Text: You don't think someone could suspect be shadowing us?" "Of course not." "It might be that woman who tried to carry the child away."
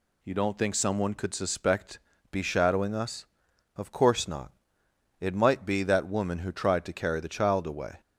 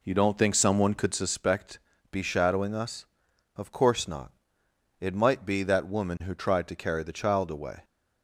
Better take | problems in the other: first | starts louder than the rest; until 1.4 s; 3.5 dB // pauses between "suspect" and "be"; slight; at 1.7 s; 0.32 s long; slight in the first

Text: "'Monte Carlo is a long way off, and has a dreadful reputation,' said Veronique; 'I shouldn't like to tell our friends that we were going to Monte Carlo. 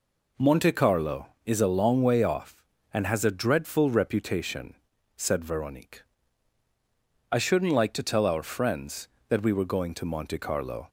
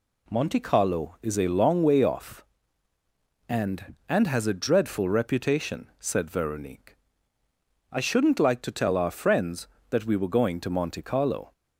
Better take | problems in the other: first | says "and" twice; at 4.0 s

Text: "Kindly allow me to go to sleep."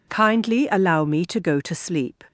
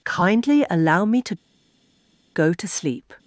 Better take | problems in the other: first | pauses between "to" and "go"; at 1.3 s; 0.99 s long

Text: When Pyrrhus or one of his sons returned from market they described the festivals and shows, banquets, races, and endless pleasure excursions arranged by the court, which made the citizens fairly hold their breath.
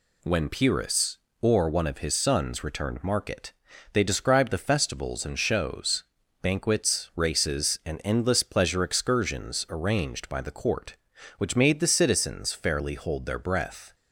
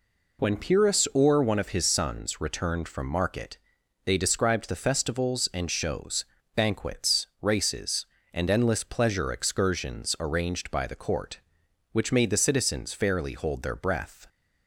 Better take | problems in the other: second | skips "from"; at 3.0 s // pauses between "market" and "they"; at 3.5 s; 0.40 s long; noticeable in the second

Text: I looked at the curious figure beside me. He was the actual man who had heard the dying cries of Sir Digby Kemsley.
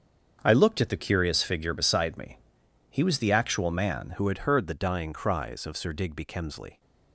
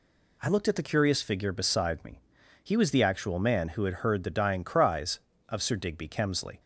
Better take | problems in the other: second | starts louder than the rest; strong; until 1.4 s; 7 dB // changes voice at "who"; from 4.1 s on; 2.6 s long

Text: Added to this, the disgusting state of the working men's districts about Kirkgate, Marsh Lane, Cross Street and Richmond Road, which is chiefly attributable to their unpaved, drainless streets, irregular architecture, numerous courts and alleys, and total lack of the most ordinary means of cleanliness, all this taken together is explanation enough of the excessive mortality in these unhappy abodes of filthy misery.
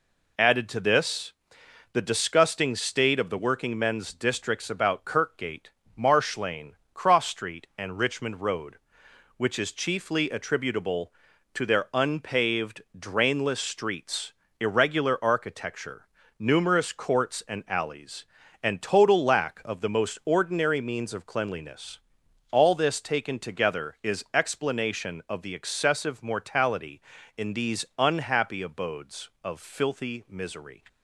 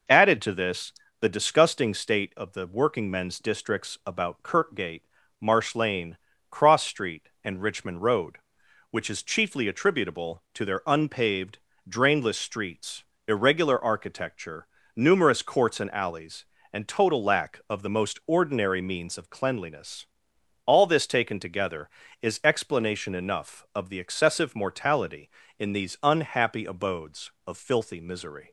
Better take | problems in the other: second | skips "enough"; at 25.2 s

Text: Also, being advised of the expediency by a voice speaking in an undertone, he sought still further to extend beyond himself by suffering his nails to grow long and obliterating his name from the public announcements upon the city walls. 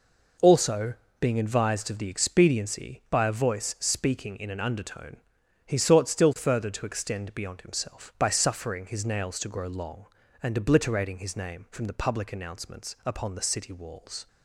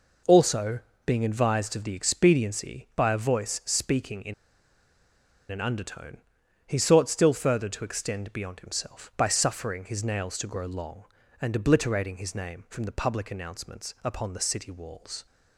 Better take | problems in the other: first | pauses between "in" and "an"; at 4.3 s; 1.1 s long

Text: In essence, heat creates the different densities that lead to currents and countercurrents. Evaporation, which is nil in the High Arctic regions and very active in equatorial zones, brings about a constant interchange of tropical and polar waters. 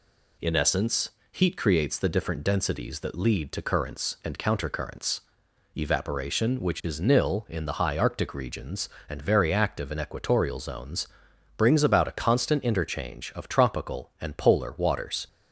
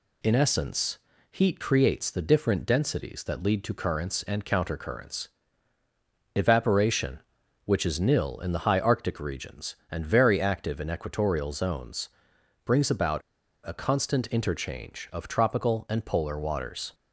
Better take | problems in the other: first | pauses between "about" and "a"; at 13.2 s; 0.45 s long

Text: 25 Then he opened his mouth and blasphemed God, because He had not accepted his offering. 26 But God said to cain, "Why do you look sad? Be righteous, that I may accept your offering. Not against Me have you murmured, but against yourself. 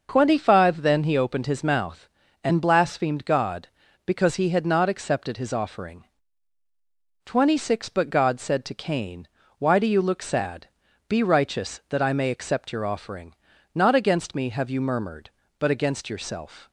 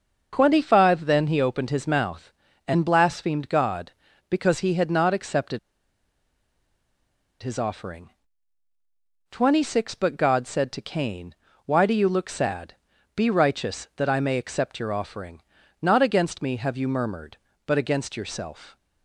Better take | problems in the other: first | starts louder than the rest; noticeable; until 1.3 s; 6 dB; noticeable in the first // pauses between "accepted" and "his"; strong; at 5.5 s; 1.8 s long

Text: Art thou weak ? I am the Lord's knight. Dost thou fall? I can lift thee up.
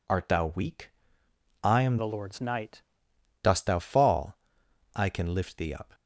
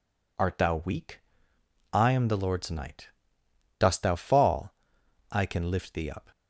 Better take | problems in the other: second | changes voice from "the" to "knight"; from 1.9 to 2.8 s; 0.9 s long

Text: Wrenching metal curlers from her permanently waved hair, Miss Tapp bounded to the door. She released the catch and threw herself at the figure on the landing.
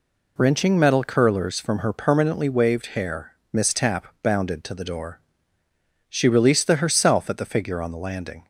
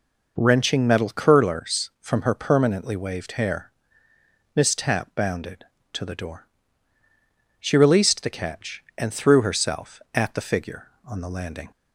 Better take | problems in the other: second | skips "catch and threw"; at 6.7 s

